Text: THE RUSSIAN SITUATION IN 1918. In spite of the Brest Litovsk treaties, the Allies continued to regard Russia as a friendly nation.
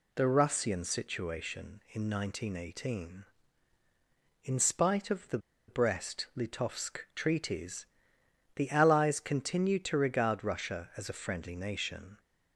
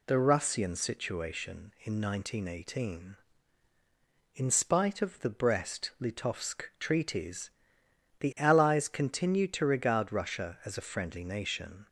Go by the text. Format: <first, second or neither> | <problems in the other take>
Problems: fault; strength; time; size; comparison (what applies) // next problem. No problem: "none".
second | pauses between "the" and "Brest"; slight; at 5.3 s; 0.29 s long